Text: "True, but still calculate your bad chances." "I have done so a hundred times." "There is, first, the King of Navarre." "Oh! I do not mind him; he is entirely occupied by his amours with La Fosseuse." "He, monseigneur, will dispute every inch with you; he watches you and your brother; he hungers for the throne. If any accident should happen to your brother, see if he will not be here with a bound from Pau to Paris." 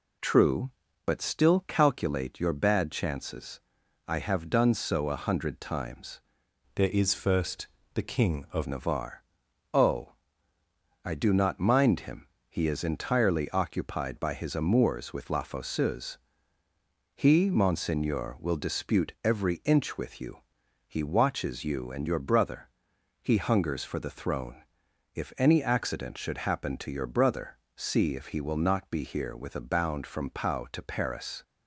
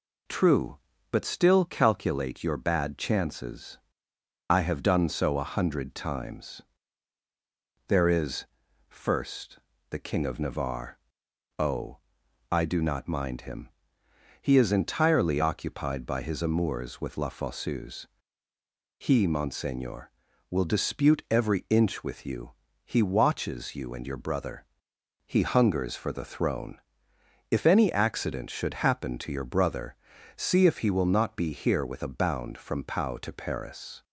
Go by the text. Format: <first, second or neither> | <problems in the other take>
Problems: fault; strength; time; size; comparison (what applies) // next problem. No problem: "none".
second | changes voice from "There" to "of"; from 6.7 to 8.6 s; 1.9 s long